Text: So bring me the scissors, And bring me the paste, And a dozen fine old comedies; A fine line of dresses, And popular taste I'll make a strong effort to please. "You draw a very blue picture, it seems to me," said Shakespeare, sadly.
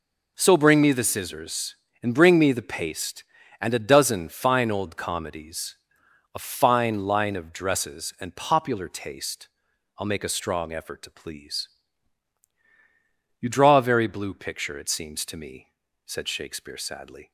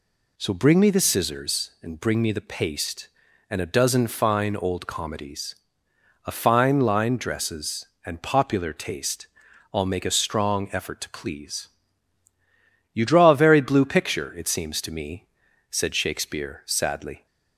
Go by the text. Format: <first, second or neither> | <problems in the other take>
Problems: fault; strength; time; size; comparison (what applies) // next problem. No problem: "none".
first | skips "of"; at 7.1 s // pauses between "taste" and "I'll"; noticeable; at 9.2 s; 0.46 s long; noticeable in the first